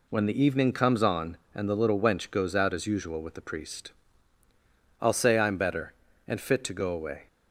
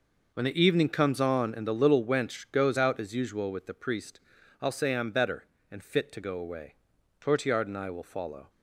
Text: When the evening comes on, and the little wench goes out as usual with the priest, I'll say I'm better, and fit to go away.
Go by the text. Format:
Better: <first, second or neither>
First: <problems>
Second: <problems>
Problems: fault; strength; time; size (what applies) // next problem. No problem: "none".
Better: first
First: none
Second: goes on to say "Tortillard and I will follow"; noticeable; from 7.1 s on; 1.3 s long